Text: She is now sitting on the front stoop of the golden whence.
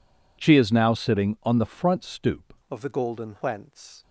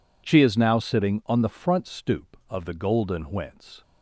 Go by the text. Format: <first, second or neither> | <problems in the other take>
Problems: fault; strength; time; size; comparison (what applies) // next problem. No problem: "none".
second | changes voice at "of"; from 2.7 s on; 1.3 s long